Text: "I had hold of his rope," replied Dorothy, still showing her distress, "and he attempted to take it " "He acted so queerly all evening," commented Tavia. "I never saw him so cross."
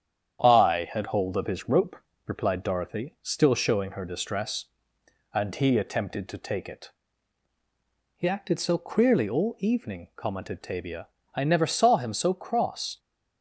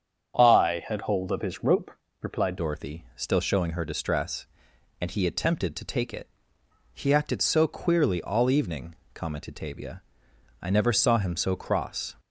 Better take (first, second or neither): first